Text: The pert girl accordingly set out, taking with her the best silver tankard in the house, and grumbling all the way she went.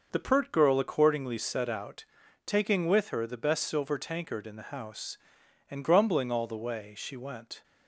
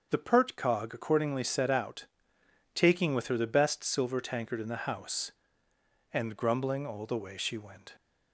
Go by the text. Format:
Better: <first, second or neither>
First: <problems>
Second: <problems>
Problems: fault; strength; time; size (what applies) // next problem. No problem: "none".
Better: first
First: starts louder than the rest; noticeable; until 1.1 s; 6 dB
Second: starts louder than the rest; until 1.1 s; 6.5 dB // says "cog" for "girl"; at 0.5 s